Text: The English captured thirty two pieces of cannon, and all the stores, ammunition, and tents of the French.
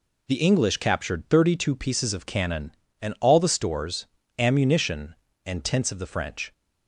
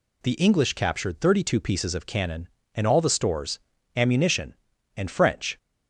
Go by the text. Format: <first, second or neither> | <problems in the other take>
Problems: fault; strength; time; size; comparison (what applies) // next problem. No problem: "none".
first | skips "tents of the"; at 5.0 s